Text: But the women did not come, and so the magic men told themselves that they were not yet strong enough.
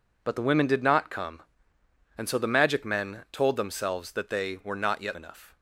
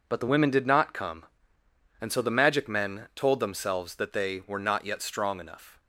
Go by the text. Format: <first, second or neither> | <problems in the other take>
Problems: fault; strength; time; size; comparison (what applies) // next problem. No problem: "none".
second | skips "strong"; at 5.1 s